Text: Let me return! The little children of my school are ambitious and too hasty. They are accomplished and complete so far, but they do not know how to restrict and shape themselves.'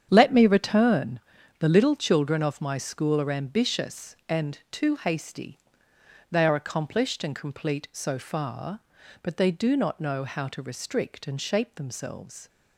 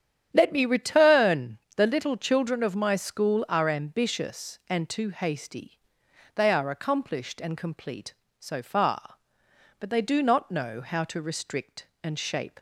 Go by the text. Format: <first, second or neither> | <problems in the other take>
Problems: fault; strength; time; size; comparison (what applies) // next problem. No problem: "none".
first | starts louder than the rest; strong; until 1.3 s; 9.5 dB; strong in the first // stops before "themselves"; at 12.5 s